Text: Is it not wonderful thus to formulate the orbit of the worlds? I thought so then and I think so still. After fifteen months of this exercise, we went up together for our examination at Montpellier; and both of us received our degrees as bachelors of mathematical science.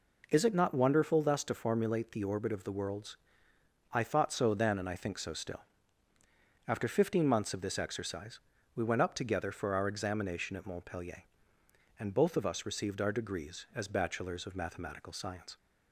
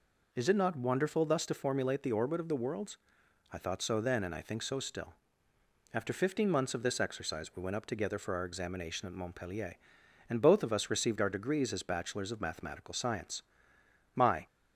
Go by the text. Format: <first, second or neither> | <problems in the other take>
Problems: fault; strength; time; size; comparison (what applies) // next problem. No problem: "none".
first | goes on to say "My"; slight; from 14.1 s on; 0.30 s long